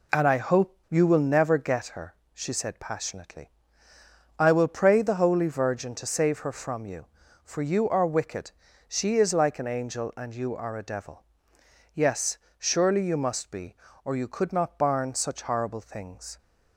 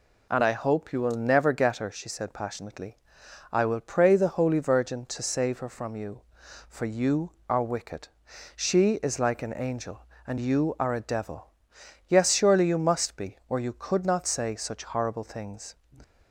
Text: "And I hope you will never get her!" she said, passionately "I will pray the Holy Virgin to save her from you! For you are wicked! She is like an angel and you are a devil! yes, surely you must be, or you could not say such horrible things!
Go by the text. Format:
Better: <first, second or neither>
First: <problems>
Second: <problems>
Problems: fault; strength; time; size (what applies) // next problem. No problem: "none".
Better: second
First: pauses between "passionately" and "I"; noticeable; at 3.4 s; 0.88 s long // says "barn" for "say"; at 14.7 s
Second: pauses between "passionately" and "I"; noticeable; at 2.9 s; 0.54 s long